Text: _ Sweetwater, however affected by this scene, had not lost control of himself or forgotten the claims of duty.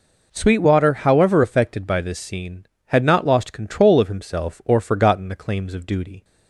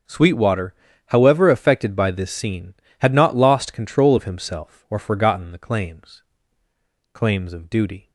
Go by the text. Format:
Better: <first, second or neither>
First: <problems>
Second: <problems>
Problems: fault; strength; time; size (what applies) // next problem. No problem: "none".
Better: first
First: none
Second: starts louder than the rest; until 1.4 s; 6.5 dB // says "claims" twice; at 7.1 s